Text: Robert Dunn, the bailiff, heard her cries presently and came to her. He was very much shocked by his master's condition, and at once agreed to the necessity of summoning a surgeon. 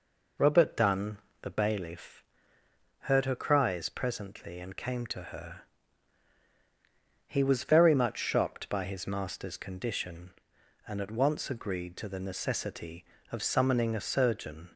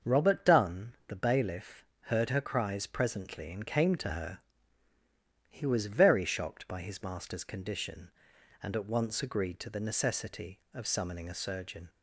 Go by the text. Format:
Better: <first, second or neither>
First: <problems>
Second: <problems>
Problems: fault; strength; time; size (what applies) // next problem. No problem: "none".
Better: first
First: none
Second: starts louder than the rest; until 1.1 s; 6.5 dB // skips "much"; at 6.2 s